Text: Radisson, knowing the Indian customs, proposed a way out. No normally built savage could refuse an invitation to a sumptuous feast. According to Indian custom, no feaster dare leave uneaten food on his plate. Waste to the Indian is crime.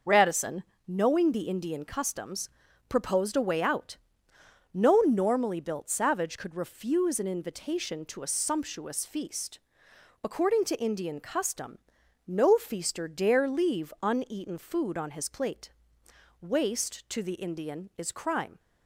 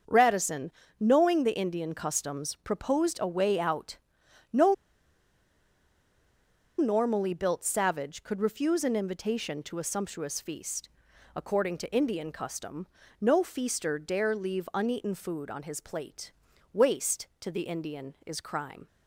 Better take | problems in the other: first | starts louder than the rest; until 1.3 s; 6.5 dB // pauses between "No" and "normally"; strong; at 4.7 s; 2.0 s long

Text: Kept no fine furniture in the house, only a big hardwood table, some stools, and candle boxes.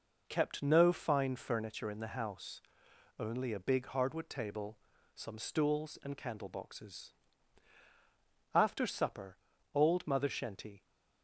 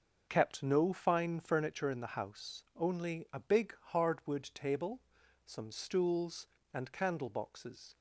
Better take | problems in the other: second | goes on to say "After supper old Mother Shenty"; strong; from 8.5 s on; 2.3 s long

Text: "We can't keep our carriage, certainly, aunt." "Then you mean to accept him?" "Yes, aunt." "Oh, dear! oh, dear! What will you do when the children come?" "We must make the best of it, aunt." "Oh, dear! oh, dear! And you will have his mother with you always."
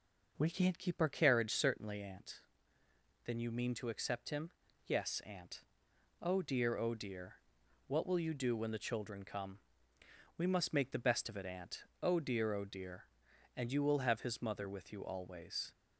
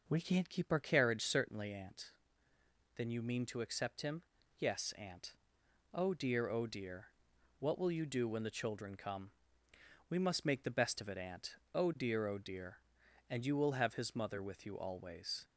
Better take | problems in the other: neither | none

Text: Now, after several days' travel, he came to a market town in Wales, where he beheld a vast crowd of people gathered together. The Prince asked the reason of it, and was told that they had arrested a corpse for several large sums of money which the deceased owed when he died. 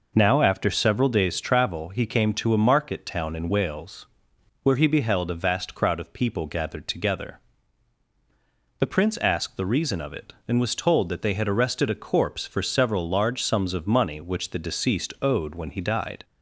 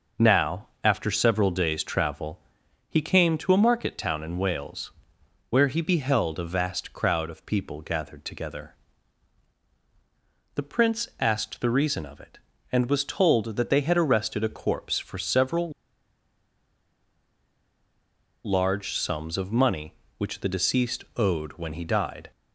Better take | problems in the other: first | pauses between "several" and "large"; strong; at 15.7 s; 2.7 s long

